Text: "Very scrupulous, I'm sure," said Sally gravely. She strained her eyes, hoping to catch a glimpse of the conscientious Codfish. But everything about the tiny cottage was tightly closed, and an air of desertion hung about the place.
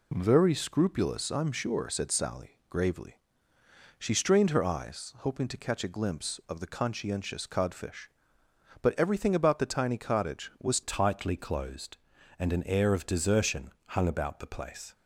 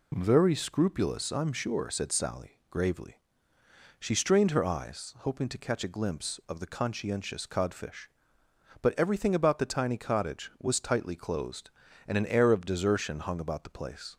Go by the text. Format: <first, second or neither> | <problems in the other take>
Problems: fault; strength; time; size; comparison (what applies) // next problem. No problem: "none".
second | changes voice at "tightly"; from 10.8 s on; 4.1 s long // pauses between "desertion" and "hung"; slight; at 13.7 s; 0.16 s long